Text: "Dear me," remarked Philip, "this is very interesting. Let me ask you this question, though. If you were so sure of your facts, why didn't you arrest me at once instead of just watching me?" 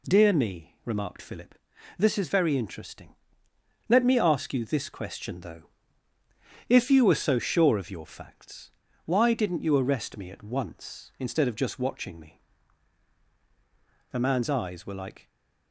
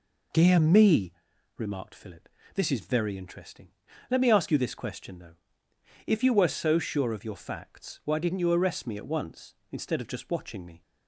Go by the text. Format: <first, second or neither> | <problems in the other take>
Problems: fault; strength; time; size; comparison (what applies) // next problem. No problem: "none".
second | goes on to say "The man's eyes were like"; noticeable; from 14.1 s on; 1.2 s long // stays silent after the last word; slight; from 15.2 s on; 0.5 s long